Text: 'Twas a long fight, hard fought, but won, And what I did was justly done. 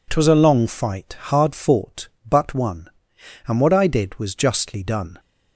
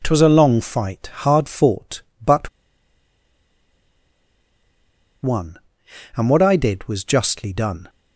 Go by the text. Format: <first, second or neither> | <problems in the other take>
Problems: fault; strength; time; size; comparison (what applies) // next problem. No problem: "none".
first | pauses between "but" and "won"; strong; at 2.4 s; 2.7 s long